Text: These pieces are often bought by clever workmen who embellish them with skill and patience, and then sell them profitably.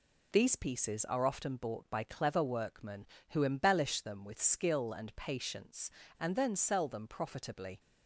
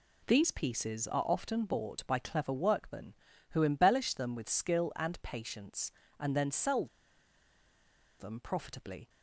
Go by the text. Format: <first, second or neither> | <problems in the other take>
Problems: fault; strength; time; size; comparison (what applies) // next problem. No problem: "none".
first | pauses between "sell" and "them"; strong; at 6.8 s; 1.3 s long